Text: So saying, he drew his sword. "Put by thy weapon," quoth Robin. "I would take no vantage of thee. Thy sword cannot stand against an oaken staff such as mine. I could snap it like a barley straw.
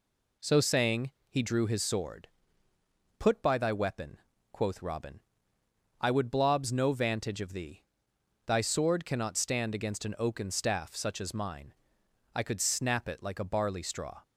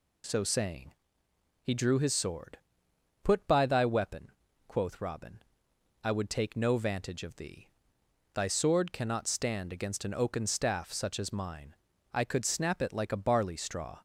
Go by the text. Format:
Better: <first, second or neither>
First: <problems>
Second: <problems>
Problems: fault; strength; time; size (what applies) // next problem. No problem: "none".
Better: second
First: says "blobs" for "take"; at 6.3 s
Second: none